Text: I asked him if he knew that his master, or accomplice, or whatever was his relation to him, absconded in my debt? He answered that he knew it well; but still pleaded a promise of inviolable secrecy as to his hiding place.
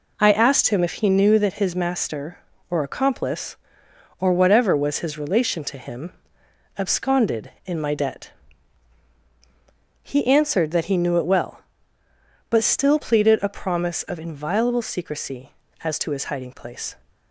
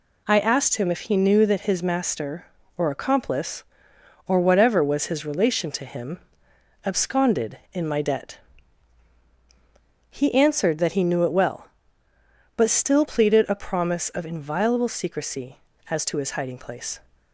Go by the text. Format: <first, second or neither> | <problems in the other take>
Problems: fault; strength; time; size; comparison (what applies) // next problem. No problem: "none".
second | starts louder than the rest; until 1.3 s; 3.5 dB